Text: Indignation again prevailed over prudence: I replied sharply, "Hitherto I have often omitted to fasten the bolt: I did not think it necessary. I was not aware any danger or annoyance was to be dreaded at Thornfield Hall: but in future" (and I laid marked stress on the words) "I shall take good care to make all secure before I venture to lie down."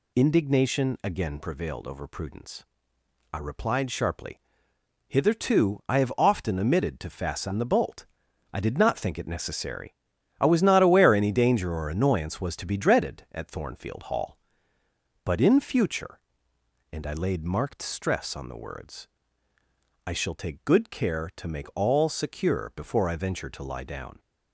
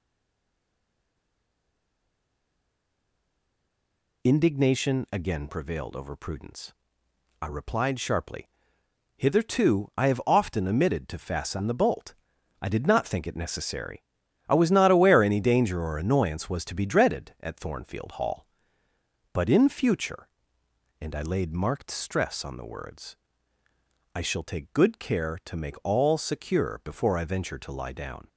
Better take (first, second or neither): first